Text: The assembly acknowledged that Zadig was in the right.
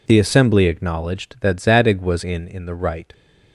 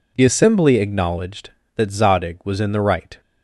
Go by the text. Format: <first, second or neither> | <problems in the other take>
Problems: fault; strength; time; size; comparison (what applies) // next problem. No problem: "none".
second | says "in" twice; at 2.4 s